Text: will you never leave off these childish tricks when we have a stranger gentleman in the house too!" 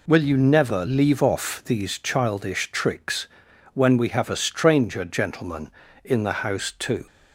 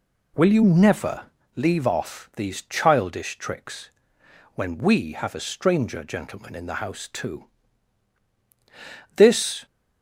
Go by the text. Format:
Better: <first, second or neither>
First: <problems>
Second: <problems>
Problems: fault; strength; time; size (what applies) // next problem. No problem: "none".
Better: first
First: pauses between "tricks" and "when"; noticeable; at 3.2 s; 0.46 s long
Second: pauses between "never" and "leave"; slight; at 1.2 s; 0.28 s long // pauses between "tricks" and "when"; noticeable; at 3.8 s; 0.66 s long // goes on to say "This"; from 9.1 s on; 0.50 s long